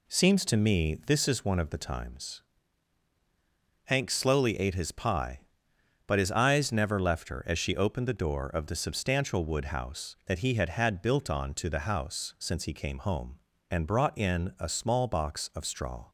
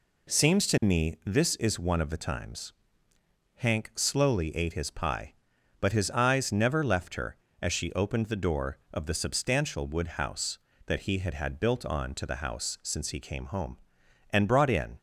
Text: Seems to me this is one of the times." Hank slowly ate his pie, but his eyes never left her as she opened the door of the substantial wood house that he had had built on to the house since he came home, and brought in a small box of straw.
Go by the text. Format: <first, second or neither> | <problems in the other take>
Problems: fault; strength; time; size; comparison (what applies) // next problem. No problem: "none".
first | stops before "a small box of straw"; at 14.9 s